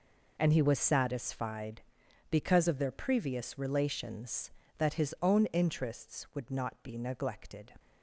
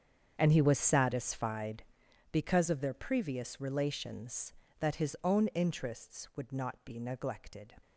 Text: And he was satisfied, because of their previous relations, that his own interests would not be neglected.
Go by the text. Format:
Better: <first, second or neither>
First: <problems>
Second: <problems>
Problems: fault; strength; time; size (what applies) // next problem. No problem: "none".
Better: first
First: none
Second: starts louder than the rest; strong; until 2.2 s; 7.5 dB